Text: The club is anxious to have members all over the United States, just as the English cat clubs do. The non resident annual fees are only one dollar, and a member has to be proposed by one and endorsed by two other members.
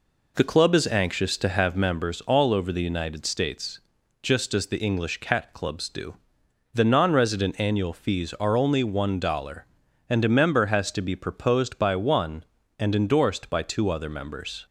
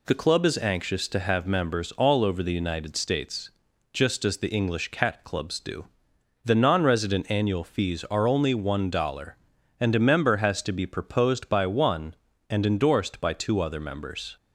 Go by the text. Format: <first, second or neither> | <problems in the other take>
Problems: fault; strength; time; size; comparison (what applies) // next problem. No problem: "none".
second | starts louder than the rest; until 2.0 s; 3.5 dB